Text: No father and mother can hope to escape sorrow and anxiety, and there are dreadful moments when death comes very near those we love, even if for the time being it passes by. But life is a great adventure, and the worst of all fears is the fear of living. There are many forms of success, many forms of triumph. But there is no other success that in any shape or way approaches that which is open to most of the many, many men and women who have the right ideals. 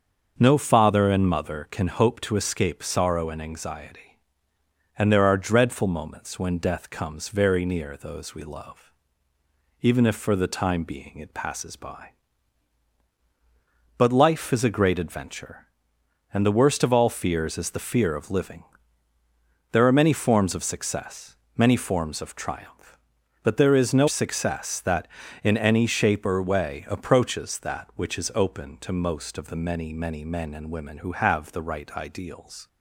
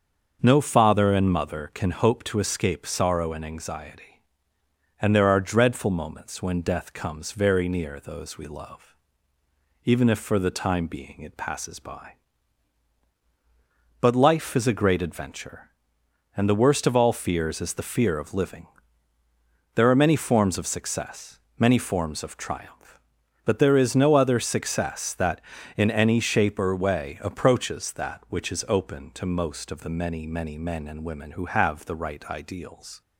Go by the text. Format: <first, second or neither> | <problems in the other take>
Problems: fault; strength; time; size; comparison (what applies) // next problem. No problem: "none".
second | starts louder than the rest; until 1.3 s; 6.5 dB; also in the second // skips "other"; at 24.0 s